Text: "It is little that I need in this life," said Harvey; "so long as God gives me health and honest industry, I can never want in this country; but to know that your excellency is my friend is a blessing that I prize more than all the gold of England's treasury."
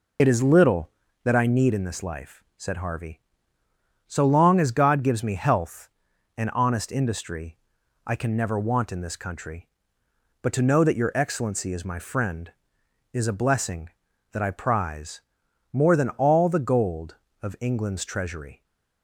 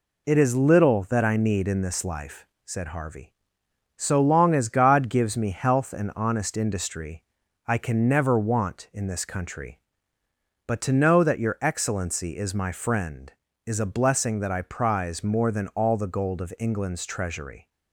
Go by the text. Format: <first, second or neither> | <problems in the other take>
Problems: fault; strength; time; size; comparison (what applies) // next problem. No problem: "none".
second | loses the start of "It"; at 0.1 s; 40 ms // pauses between "prize" and "more"; noticeable; at 15.1 s; 0.52 s long